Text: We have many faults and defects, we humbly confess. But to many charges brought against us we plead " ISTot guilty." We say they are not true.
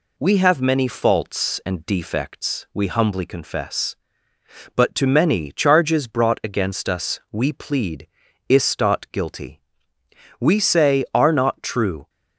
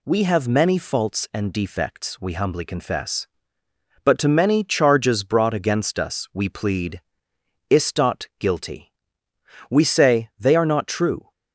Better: second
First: skips "they"; at 11.1 s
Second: none

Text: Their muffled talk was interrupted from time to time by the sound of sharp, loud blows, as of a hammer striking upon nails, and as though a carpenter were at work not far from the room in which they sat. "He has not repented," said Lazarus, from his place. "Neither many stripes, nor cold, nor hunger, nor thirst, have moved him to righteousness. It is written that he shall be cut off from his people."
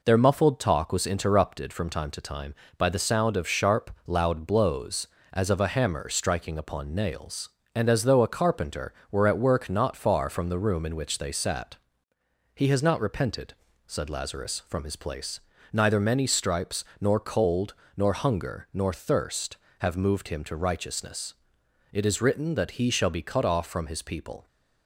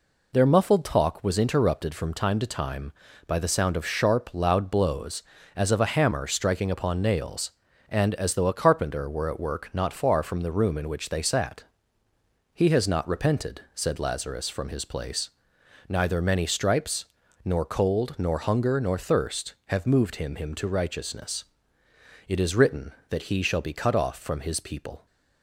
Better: first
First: none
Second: says "him" twice; at 20.3 s

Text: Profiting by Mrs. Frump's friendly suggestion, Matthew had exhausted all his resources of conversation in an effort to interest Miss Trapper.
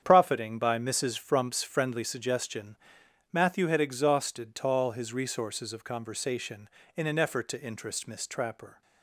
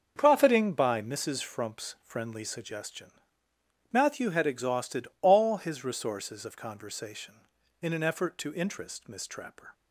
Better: second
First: starts louder than the rest; strong; until 1.0 s; 8.5 dB // says "tall" for "all"; at 4.5 s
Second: starts louder than the rest; until 1.1 s; 7 dB

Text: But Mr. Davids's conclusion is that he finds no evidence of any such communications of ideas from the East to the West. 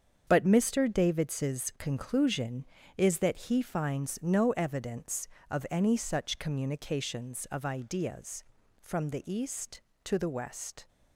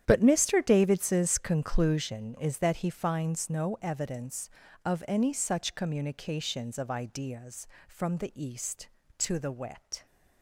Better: first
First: starts louder than the rest; strong; until 1.2 s; 7.5 dB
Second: starts louder than the rest; strong; until 1.0 s; 10 dB // says "Wet" for "West"; at 9.5 s

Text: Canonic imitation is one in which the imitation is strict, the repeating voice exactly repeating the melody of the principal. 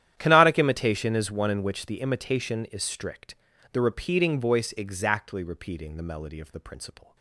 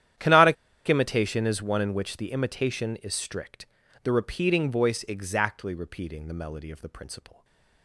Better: first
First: starts louder than the rest; strong; until 1.1 s; 11 dB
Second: starts louder than the rest; strong; until 1.5 s; 11 dB // pauses between "Canonic" and "imitation"; slight; at 0.5 s; 0.33 s long // stays silent after the last word; slight; from 7.3 s on; 0.5 s long

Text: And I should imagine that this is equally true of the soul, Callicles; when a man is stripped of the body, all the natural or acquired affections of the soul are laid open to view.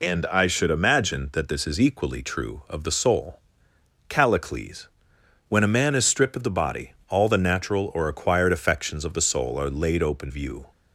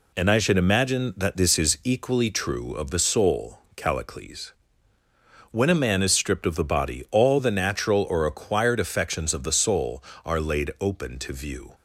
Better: second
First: skips "to"; at 10.3 s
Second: none

